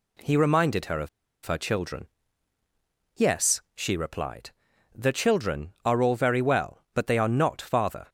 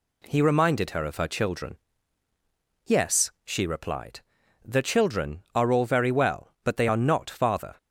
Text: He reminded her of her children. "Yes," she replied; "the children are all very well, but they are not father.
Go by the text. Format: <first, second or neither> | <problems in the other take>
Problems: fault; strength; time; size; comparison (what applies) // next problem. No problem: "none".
second | pauses between "of" and "her"; at 1.0 s; 0.36 s long